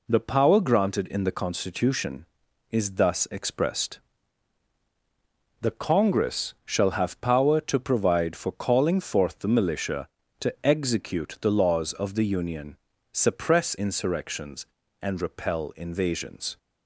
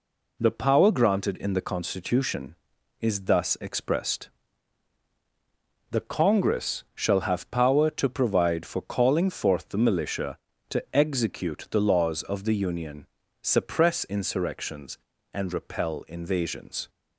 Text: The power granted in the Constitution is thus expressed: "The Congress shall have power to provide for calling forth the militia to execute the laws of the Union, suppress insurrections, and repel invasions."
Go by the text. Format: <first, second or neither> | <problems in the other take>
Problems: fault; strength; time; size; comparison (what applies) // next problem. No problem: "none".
neither | none